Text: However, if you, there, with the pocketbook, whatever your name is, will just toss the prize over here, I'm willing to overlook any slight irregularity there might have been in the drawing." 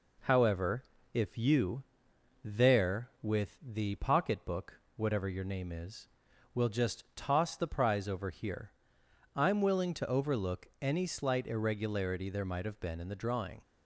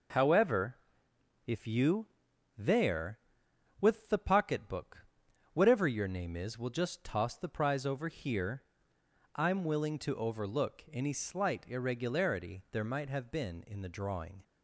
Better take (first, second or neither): neither